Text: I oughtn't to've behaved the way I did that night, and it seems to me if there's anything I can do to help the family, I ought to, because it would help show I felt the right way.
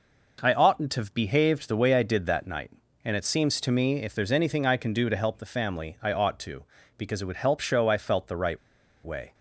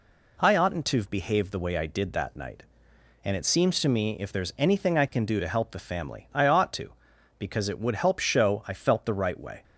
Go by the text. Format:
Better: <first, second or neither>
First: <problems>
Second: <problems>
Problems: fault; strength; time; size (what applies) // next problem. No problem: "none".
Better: second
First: pauses between "right" and "way"; noticeable; at 8.5 s; 0.47 s long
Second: none